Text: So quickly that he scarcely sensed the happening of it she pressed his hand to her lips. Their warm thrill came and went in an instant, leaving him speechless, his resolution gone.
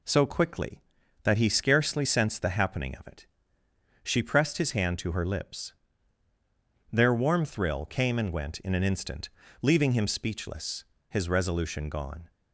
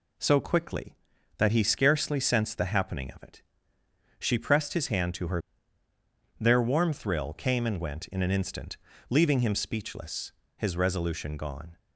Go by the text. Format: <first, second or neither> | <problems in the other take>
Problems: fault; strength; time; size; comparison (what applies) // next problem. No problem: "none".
first | pauses between "it" and "she"; noticeable; at 3.4 s; 0.76 s long; noticeable in the first // skips "lips"; at 5.8 s